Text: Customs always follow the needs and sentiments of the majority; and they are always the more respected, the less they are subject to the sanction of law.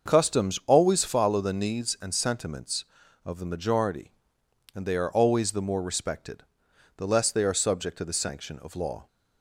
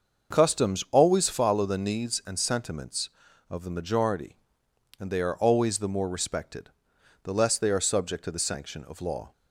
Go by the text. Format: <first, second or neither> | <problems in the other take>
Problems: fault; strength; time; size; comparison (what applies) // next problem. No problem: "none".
neither | starts louder than the rest; the same in both